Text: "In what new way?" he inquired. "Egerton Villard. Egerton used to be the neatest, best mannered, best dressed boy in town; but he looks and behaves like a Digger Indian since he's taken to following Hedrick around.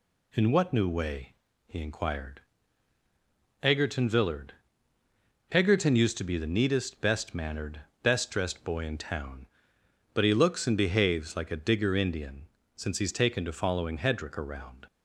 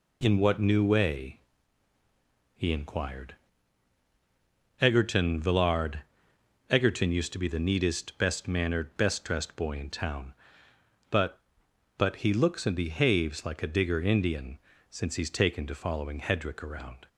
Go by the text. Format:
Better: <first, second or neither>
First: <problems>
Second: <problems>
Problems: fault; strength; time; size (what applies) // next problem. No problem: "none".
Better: first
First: pauses between "Indian" and "since"; slight; at 12.4 s; 0.28 s long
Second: says "but" twice; at 11.9 s // pauses between "Indian" and "since"; slight; at 14.5 s; 0.32 s long